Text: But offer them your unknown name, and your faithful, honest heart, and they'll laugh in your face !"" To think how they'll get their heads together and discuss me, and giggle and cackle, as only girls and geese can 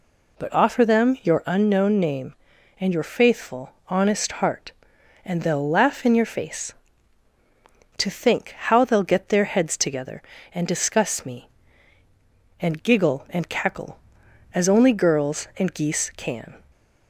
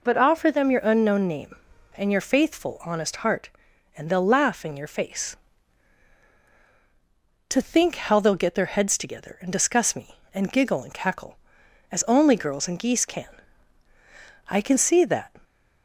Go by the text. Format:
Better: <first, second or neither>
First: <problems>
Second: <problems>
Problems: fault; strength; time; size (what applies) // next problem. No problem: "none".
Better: first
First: none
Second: goes on to say "I can see that"; noticeable; from 14.4 s on; 0.84 s long